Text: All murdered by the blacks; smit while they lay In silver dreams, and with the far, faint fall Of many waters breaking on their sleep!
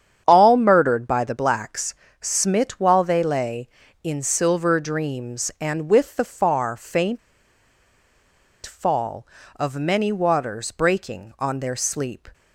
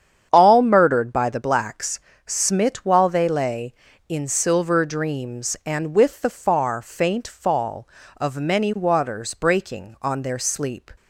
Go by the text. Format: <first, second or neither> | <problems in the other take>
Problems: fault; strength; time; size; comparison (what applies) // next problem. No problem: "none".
second | starts louder than the rest; strong; until 1.2 s; 8.5 dB; strong in the second // pauses between "faint" and "fall"; strong; at 7.1 s; 1.4 s long